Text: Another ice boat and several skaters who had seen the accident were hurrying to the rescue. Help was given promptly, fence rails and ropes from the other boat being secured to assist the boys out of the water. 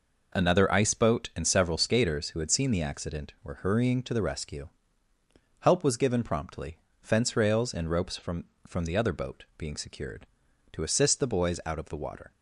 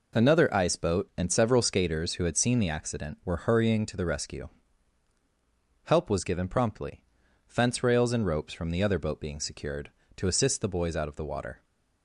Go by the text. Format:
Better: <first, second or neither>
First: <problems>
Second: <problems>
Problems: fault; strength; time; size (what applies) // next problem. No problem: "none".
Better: second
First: says "from" twice; at 8.6 s // pauses between "boat" and "being"; slight; at 9.4 s; 0.16 s long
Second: none